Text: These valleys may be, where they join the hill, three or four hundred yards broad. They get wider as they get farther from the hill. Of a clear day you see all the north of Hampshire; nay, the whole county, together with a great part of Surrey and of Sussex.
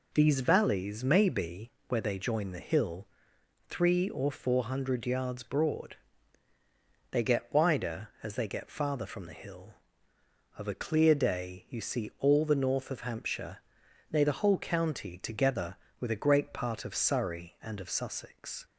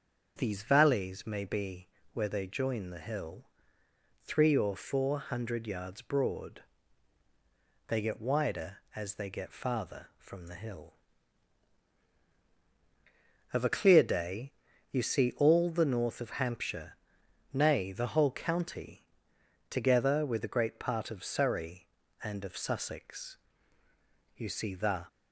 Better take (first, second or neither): first